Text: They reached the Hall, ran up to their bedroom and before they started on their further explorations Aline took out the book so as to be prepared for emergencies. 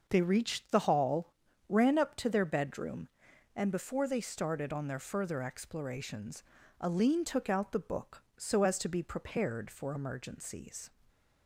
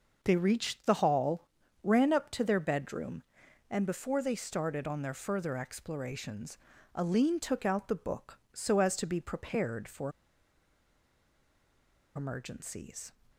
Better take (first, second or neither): first